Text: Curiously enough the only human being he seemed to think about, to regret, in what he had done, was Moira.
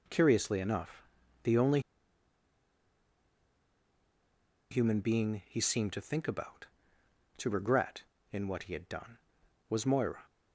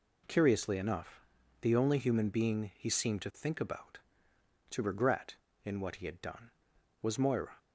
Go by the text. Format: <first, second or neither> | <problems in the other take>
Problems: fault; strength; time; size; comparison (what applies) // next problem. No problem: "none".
second | pauses between "enough" and "the"; at 1.0 s; 0.40 s long; also in the second // pauses between "only" and "human"; strong; at 1.7 s; 2.9 s long